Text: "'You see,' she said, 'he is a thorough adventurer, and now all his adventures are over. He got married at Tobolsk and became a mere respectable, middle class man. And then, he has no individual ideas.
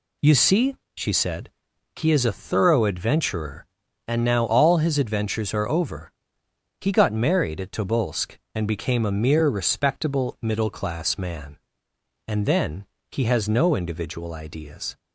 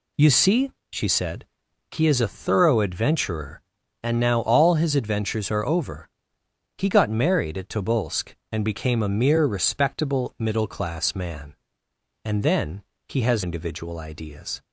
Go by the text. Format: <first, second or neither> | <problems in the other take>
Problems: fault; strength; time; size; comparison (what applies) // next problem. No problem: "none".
first | skips "no"; at 13.4 s